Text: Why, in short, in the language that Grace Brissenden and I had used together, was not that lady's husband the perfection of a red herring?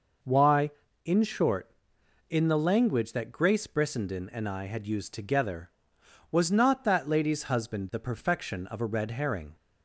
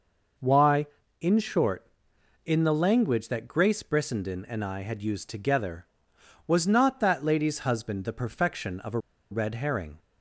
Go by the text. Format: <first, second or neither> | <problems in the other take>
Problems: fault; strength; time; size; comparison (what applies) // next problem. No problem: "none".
first | pauses between "a" and "red"; slight; at 8.9 s; 0.32 s long